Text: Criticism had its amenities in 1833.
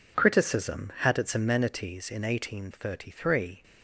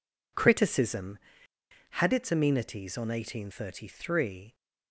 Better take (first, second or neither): first